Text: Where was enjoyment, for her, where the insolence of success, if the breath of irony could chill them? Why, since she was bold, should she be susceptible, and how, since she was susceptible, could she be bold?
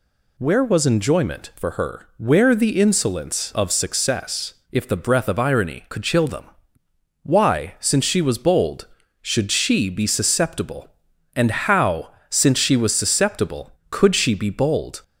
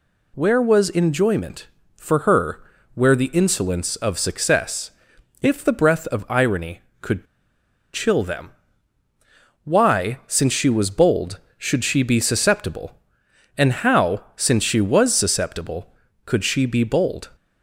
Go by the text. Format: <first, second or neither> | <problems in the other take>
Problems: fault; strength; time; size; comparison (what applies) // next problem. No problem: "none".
first | pauses between "could" and "chill"; noticeable; at 7.2 s; 0.68 s long